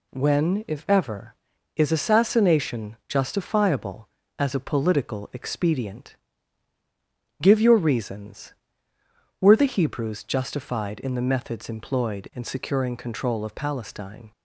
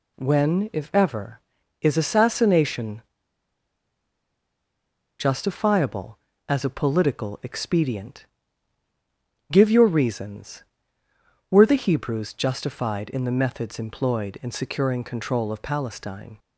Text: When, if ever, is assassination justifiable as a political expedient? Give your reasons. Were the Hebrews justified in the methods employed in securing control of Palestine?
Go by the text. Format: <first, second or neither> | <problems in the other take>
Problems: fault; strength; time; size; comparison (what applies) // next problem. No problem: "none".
first | pauses between "assassination" and "justifiable"; strong; at 3.0 s; 2.1 s long